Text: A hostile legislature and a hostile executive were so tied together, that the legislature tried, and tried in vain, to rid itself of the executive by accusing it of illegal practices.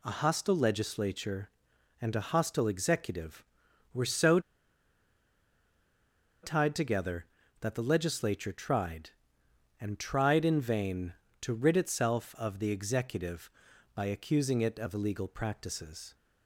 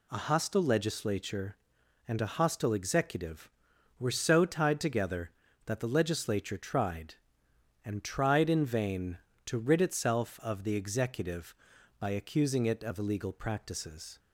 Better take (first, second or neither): second